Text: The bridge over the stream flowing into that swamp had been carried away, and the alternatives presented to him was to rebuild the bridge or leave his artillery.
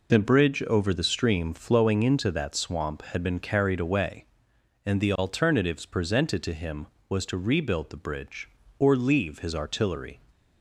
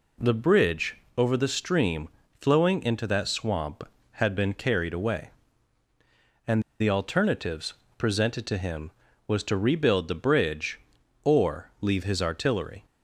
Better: first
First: none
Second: pauses between "bridge" and "over"; slight; at 0.9 s; 0.20 s long // pauses between "stream" and "flowing"; slight; at 2.0 s; 0.32 s long // pauses between "and" and "the"; slight; at 6.6 s; 0.19 s long // pauses between "alternatives" and "presented"; slight; at 7.7 s; 0.24 s long

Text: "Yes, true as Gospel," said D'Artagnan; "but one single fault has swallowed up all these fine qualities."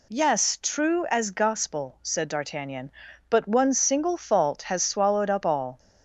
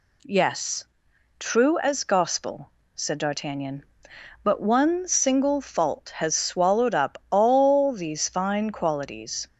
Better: second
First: stops before "these fine qualities"; at 5.7 s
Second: none

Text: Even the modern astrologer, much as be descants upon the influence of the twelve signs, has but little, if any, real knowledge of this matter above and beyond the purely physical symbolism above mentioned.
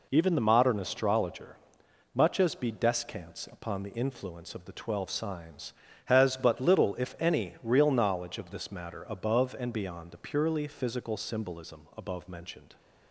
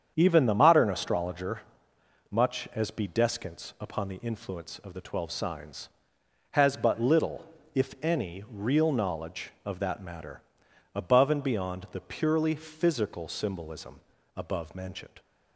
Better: first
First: none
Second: starts louder than the rest; strong; until 1.1 s; 8 dB // says "that" for "this"; at 9.8 s // pauses between "matter" and "above"; noticeable; at 10.4 s; 0.54 s long // pauses between "symbolism" and "above"; at 13.9 s; 0.38 s long

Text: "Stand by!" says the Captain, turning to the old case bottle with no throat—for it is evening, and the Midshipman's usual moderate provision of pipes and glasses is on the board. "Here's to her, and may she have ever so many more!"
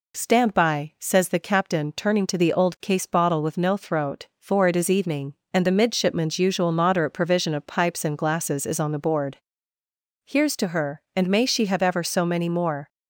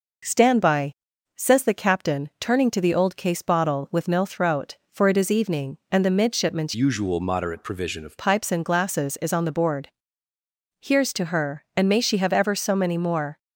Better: first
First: none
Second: changes voice from "usual" to "of"; from 6.7 to 8.1 s; 1.4 s long

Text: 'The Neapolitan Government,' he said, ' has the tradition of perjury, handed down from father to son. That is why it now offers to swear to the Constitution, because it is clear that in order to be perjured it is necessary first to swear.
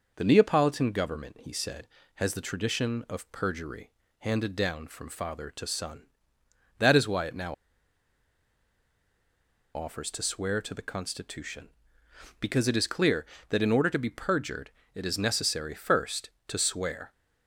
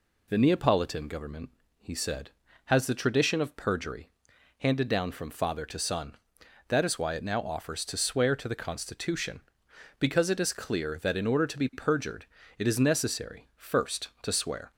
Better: second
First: pauses between "now" and "offers"; strong; at 7.5 s; 2.2 s long // pauses between "perjured" and "it"; slight; at 14.6 s; 0.24 s long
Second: pauses between "perjured" and "it"; slight; at 12.2 s; 0.32 s long

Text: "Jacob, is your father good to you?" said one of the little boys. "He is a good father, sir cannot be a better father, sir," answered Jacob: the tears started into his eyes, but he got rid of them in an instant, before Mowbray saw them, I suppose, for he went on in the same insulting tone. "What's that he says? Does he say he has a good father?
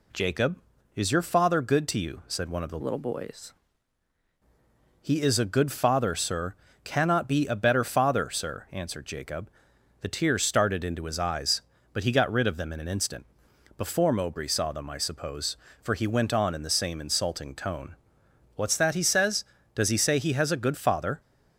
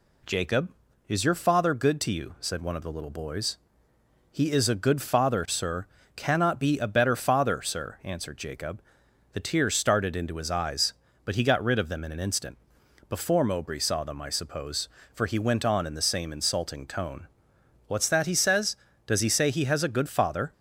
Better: second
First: changes voice from "little" to "boys"; from 2.8 to 3.5 s; 0.7 s long // pauses between "sir" and "cannot"; slight; at 6.5 s; 0.30 s long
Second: pauses between "sir" and "cannot"; slight; at 5.8 s; 0.30 s long

